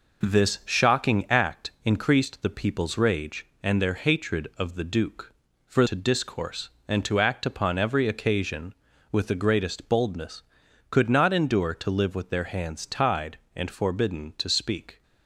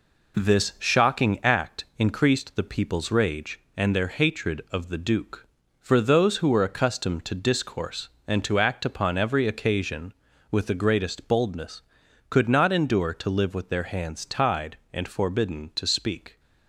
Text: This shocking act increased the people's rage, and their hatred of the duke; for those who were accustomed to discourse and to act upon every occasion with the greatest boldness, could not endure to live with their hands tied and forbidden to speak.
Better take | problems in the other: second | skips "those who were accustomed"; at 5.8 s

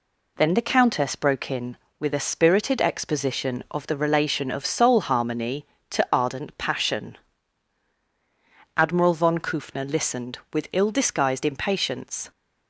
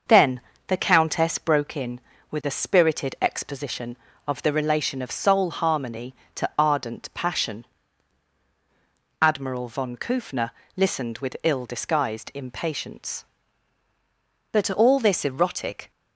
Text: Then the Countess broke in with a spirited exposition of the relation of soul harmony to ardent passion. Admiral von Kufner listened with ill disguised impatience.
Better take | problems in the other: first | starts louder than the rest; noticeable; until 1.3 s; 6 dB // pauses between "Then" and "the"; slight; at 0.4 s; 0.28 s long // pauses between "Kufner" and "listened"; slight; at 10.5 s; 0.26 s long // goes on to say "But all this erotic"; from 14.5 s on; 1.3 s long

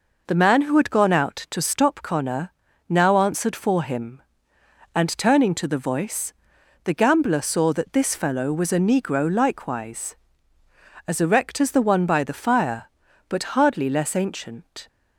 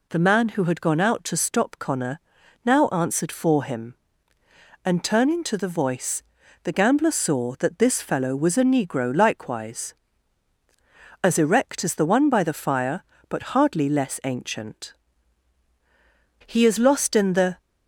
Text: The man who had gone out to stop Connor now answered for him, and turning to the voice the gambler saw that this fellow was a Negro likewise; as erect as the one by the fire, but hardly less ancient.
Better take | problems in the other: first | pauses between "Connor" and "now"; at 2.1 s; 0.44 s long; also in the first // pauses between "voice" and "the"; at 6.2 s; 0.40 s long; noticeable in the first // goes on to say "He is lost in the"; noticeable; from 16.4 s on; 1.1 s long

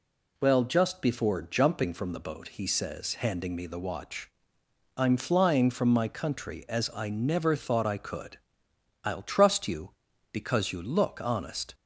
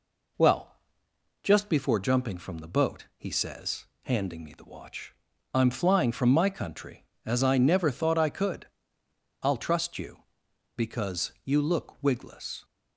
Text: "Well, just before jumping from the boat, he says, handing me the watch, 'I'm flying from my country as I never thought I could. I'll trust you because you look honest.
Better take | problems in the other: first | says "wigless" for "honest"; at 12.0 s

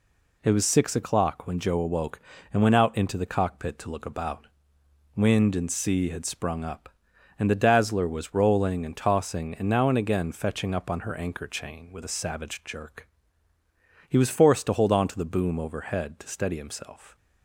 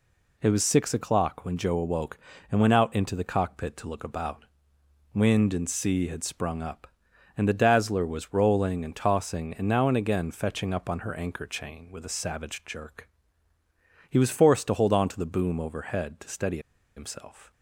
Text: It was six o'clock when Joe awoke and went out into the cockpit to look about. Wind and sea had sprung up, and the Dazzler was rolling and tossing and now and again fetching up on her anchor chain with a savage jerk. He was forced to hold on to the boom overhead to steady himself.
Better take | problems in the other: first | pauses between "steady" and "himself"; at 16.5 s; 0.37 s long

